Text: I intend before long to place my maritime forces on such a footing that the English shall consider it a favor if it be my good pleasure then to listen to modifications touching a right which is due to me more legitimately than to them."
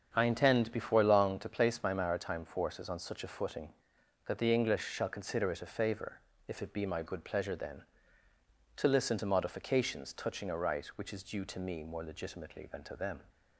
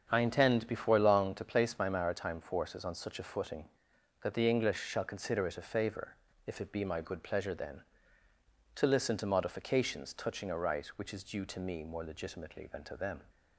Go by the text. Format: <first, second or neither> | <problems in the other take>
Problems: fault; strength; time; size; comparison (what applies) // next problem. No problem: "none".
neither | starts louder than the rest; the same in both // pauses between "favor" and "if"; slight; the same in both